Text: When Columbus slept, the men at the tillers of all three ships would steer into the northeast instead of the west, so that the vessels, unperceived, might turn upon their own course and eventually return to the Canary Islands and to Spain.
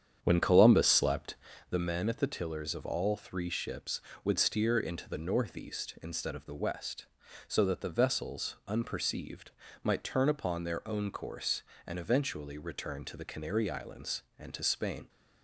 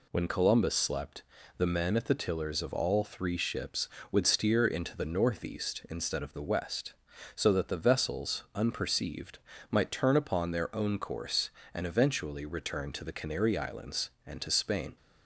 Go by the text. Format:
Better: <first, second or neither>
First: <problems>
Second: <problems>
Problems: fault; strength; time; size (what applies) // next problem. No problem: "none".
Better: second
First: starts louder than the rest; strong; until 1.6 s; 8.5 dB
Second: none